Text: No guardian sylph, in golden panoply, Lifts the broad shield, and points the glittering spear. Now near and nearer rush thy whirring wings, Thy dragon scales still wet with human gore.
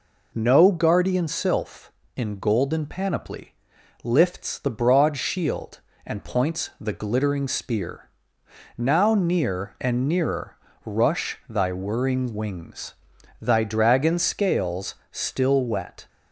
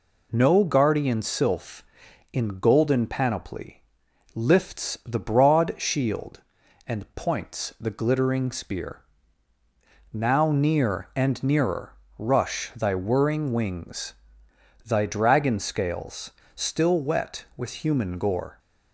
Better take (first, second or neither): second